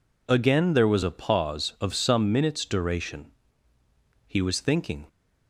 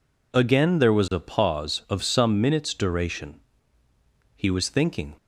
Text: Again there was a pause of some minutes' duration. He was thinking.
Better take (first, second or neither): neither